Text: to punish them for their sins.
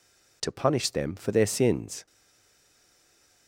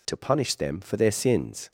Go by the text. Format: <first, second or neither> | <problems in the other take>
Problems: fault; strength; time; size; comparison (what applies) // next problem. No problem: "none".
second | stays silent after the last word; noticeable; from 2.0 s on; 1.4 s long